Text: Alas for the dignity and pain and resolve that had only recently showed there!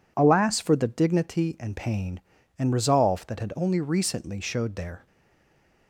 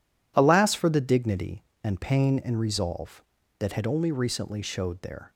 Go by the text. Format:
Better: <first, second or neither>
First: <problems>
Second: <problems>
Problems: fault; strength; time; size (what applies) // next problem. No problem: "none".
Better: second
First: stays silent after the last word; slight; from 5.0 s on; 0.8 s long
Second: none